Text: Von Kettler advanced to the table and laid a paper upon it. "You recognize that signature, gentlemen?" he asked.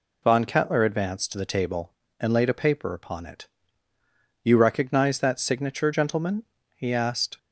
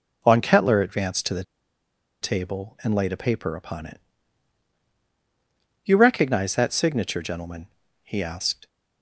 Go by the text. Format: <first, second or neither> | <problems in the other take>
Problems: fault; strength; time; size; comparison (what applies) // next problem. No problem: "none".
first | pauses between "the" and "table"; noticeable; at 1.4 s; 0.79 s long